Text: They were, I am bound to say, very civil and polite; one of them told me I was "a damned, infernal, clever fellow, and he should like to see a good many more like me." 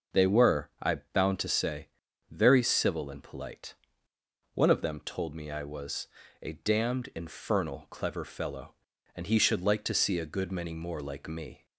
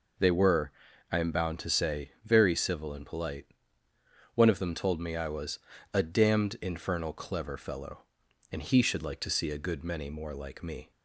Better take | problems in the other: second | skips "am"; at 1.0 s // pauses between "was" and "a"; slight; at 6.0 s; 0.34 s long; slight in the second

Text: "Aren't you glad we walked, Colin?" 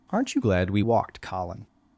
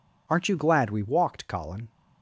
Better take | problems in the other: second | changes voice from "glad" to "we"; from 0.4 to 0.8 s; 0.4 s long

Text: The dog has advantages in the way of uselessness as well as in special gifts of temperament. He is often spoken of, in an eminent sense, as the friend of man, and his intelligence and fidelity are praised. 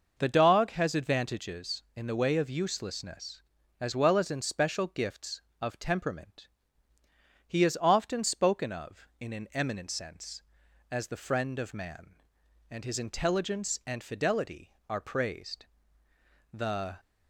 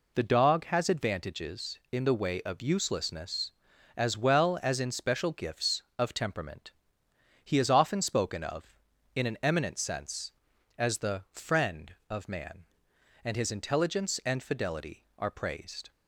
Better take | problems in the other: second | goes on to say "The"; slight; from 16.5 s on; 0.46 s long

